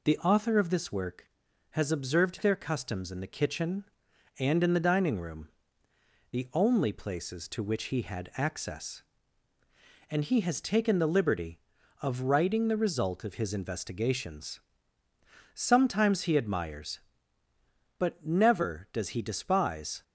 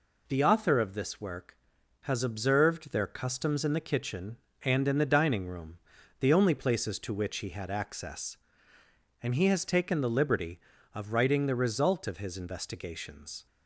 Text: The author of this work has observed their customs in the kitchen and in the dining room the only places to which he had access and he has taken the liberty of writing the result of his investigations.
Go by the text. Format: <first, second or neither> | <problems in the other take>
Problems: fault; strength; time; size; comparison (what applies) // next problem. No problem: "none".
second | pauses between "room" and "the"; noticeable; at 5.4 s; 0.82 s long; also in the second // goes on to say "Sometimes he admires but never does he despise"; strong; from 15.5 s on; 4.4 s long